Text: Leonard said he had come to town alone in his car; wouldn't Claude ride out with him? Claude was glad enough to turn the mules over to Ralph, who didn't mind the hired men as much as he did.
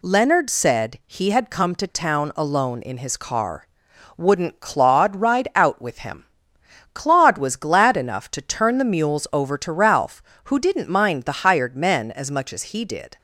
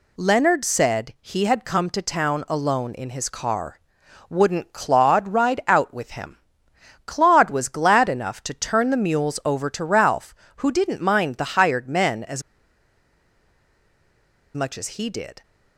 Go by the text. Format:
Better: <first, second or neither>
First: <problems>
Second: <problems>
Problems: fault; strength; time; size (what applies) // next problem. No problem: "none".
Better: first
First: none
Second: pauses between "as" and "much"; strong; at 12.4 s; 2.1 s long